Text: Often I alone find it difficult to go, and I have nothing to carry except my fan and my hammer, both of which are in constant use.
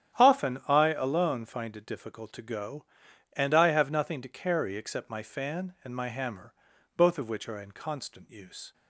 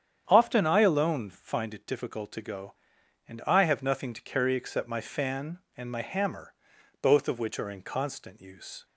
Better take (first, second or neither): neither